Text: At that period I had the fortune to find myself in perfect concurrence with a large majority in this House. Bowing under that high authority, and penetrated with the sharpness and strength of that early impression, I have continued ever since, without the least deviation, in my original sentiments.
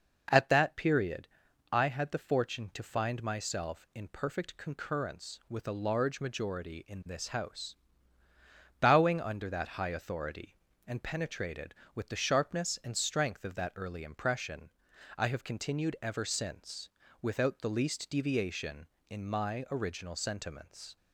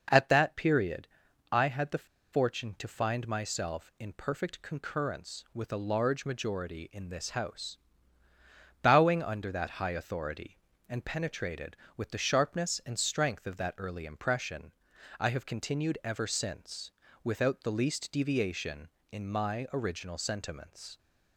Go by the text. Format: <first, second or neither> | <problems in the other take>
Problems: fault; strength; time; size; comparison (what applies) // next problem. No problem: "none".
first | pauses between "period" and "I"; at 1.0 s; 0.44 s long; also in the first // pauses between "the" and "fortune"; slight; at 2.0 s; 0.27 s long